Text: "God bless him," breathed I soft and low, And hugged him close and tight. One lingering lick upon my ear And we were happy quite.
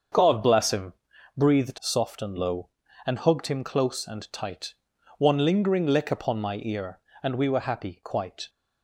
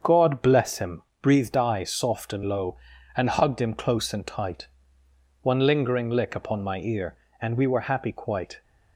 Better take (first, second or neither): second